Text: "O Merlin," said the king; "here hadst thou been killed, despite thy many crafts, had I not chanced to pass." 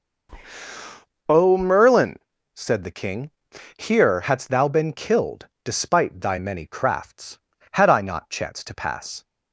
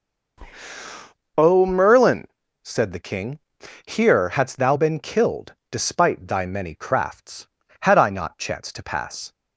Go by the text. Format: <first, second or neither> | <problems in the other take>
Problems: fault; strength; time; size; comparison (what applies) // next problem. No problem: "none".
neither | none